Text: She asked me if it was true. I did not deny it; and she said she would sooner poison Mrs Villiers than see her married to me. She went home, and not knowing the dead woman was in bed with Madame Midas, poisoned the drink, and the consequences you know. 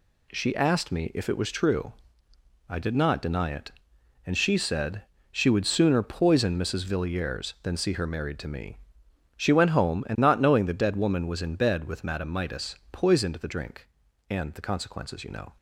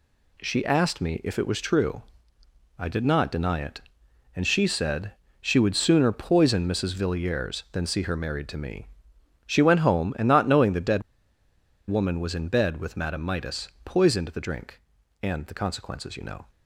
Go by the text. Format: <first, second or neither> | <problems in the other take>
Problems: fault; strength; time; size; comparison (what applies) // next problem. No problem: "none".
first | pauses between "said" and "she"; slight; at 5.1 s; 0.28 s long; slight in the first // pauses between "dead" and "woman"; noticeable; at 11.0 s; 0.87 s long